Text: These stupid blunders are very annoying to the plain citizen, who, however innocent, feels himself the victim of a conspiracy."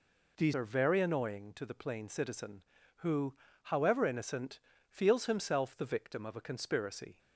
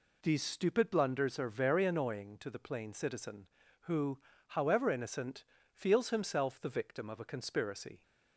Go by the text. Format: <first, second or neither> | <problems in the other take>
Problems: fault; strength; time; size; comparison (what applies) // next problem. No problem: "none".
second | skips "stupid blunders"; at 0.5 s